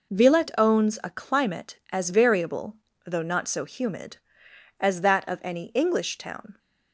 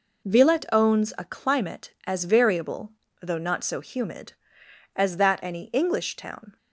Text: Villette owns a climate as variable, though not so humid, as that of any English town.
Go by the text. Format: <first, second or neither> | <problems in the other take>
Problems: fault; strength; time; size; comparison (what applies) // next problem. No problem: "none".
first | skips "of"; at 5.4 s